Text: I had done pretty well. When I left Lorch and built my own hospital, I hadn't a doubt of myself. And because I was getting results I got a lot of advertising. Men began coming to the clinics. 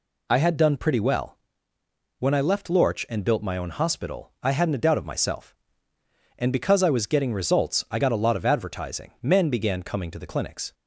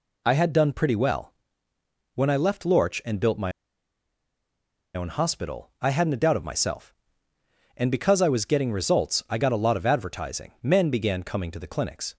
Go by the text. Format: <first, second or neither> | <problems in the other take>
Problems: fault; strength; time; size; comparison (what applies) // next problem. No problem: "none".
first | pauses between "my" and "own"; strong; at 3.5 s; 1.4 s long